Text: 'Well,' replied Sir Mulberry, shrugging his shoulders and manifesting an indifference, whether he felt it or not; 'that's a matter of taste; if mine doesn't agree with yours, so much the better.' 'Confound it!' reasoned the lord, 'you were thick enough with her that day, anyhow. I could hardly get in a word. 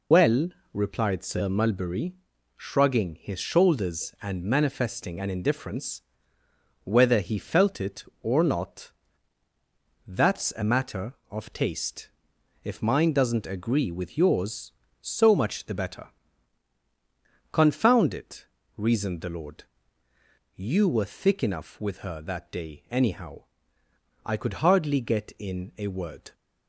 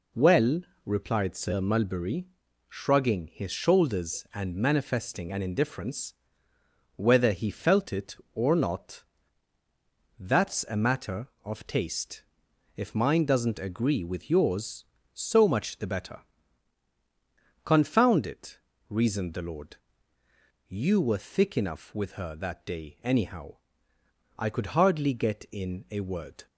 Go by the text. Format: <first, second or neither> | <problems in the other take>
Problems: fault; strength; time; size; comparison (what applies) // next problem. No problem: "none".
second | loses the start of "Well"; at 0.1 s; 80 ms